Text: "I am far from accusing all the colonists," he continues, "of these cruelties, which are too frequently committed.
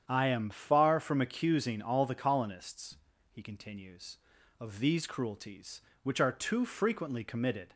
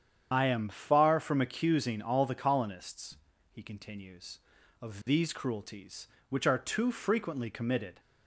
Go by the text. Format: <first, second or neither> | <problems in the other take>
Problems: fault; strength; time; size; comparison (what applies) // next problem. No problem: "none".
first | loses the start of "I"; at 0.3 s; 45 ms // starts louder than the rest; strong; until 1.3 s; 8.5 dB; strong in the first